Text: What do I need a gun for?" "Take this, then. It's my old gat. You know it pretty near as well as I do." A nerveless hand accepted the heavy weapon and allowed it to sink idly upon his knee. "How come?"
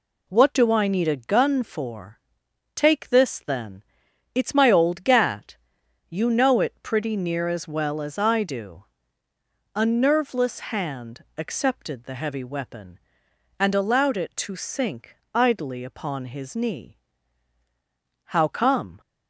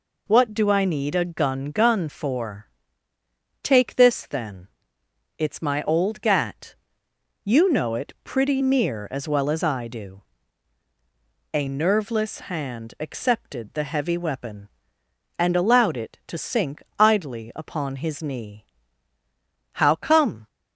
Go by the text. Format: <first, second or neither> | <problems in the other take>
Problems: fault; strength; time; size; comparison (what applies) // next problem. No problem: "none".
first | says "gun" twice; at 1.7 s // pauses between "sink" and "idly"; slight; at 16.8 s; 0.18 s long; slight in the first